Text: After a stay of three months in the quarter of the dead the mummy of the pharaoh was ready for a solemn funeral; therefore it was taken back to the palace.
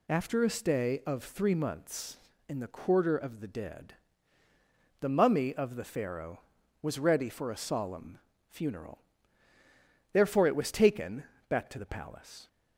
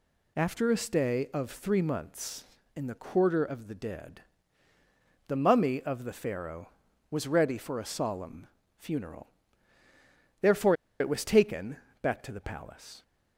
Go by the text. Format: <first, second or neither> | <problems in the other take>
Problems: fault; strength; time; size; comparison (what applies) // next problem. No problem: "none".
first | pauses between "dead" and "the"; at 4.2 s; 1.0 s long; also in the first // pauses between "solemn" and "funeral"; slight; at 8.4 s; 0.32 s long; slight in the first // pauses between "therefore" and "it"; slight; at 10.7 s; 0.26 s long // pauses between "taken" and "back"; slight; at 11.7 s; 0.24 s long; slight in the first